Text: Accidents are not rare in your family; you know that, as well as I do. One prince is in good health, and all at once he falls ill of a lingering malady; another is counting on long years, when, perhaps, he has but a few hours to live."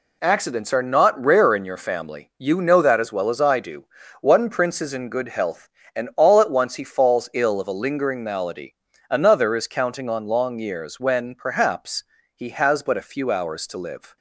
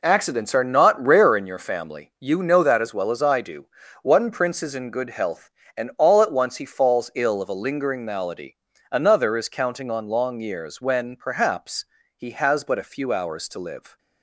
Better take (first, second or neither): first